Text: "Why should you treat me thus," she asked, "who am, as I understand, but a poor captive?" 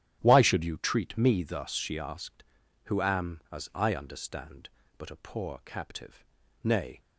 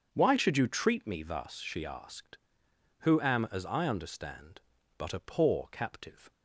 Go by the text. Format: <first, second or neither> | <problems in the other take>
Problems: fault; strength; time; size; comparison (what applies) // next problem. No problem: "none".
second | starts louder than the rest; strong; until 1.2 s; 10.5 dB; also in the second // goes on to say "Nay"; slight; from 6.6 s on; 0.38 s long